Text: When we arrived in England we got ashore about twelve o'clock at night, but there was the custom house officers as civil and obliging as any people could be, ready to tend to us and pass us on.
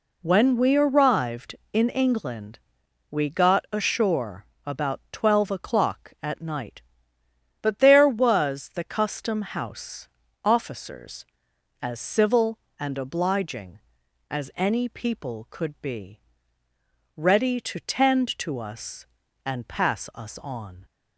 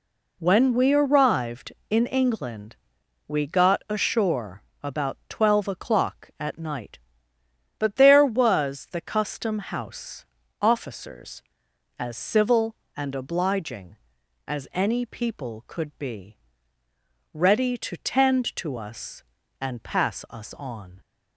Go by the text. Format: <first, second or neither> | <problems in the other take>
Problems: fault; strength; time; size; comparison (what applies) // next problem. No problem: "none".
neither | pauses between "England" and "we"; noticeable; the same in both // pauses between "ashore" and "about"; slight; the same in both // pauses between "house" and "officers"; slight; the same in both